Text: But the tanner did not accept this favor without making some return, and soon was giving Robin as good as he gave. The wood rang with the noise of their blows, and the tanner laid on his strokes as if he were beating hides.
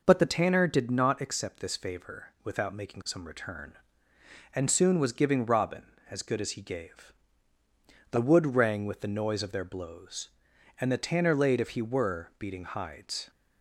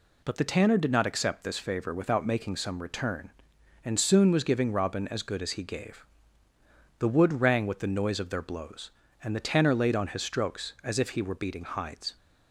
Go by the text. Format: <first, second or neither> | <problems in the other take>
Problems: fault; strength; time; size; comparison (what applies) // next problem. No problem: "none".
second | skips "on his strokes as"; at 11.5 s